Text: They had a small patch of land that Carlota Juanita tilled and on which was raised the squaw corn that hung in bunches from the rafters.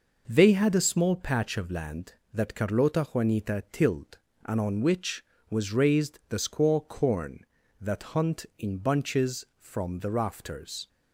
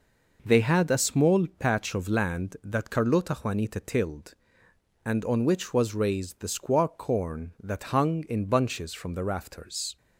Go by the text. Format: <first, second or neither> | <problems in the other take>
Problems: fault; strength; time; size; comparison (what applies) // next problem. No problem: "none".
second | says "hunt" for "hung"; at 8.1 s